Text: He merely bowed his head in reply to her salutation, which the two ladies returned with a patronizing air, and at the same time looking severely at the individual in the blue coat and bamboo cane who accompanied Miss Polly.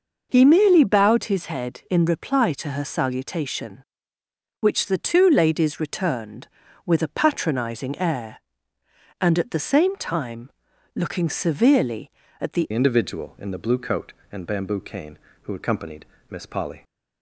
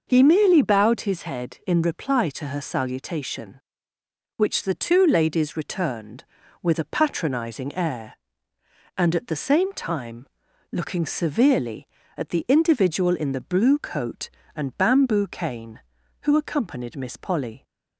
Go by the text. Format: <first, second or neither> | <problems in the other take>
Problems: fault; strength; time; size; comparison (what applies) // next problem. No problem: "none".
second | pauses between "time" and "looking"; noticeable; at 10.4 s; 0.46 s long; noticeable in the second // changes voice at "individual"; from 12.7 s on; 4.1 s long // pauses between "accompanied" and "Miss"; slight; at 16.0 s; 0.24 s long